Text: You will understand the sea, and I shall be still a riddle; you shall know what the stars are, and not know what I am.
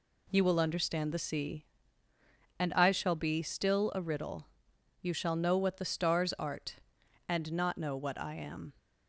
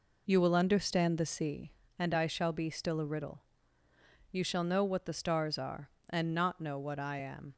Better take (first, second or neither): second